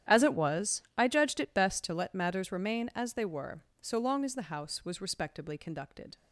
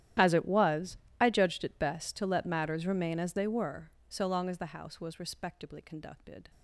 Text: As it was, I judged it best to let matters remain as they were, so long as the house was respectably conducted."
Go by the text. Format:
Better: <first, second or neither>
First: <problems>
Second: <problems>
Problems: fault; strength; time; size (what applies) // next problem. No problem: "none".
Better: first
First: starts louder than the rest; strong; until 1.2 s; 11 dB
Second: gets quieter; strong; throughout; 23 dB // starts louder than the rest; strong; until 1.4 s; 12 dB